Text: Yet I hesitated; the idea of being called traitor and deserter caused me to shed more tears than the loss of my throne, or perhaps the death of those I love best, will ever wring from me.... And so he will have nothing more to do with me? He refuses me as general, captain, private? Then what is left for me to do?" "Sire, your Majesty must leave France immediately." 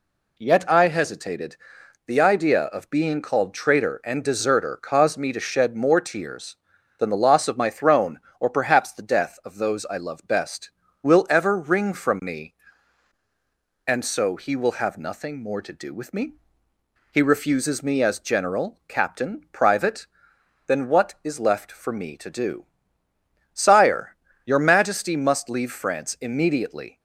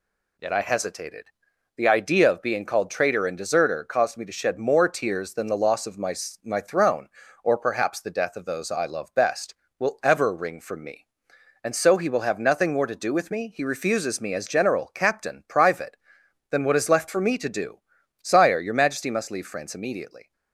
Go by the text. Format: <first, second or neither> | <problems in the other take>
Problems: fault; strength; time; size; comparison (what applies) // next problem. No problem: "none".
first | says "my" twice; at 6.4 s